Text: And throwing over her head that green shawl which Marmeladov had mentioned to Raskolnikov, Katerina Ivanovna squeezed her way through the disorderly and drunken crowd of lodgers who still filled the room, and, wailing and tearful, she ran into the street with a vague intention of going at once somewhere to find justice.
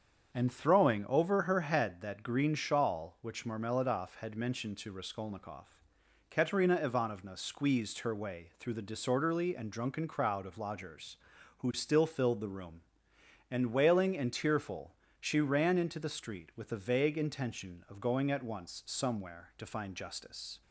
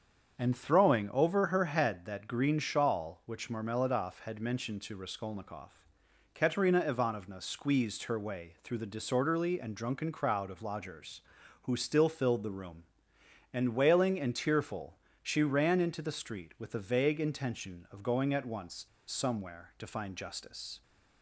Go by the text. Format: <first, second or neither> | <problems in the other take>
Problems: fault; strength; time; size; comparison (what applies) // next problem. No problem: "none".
first | starts louder than the rest; until 1.4 s; 7 dB; also in the first // pauses between "once" and "somewhere"; slight; at 18.8 s; 0.21 s long